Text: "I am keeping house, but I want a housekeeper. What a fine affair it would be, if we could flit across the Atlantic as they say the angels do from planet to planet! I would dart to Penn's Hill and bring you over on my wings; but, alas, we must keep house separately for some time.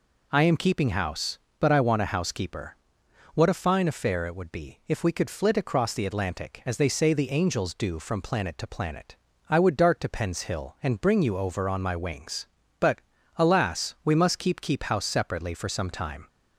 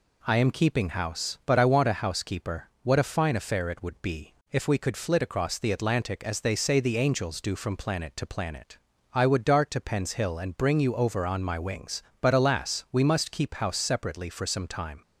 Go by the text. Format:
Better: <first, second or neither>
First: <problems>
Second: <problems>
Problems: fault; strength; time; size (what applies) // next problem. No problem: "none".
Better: second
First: says "keep" twice; at 14.5 s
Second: none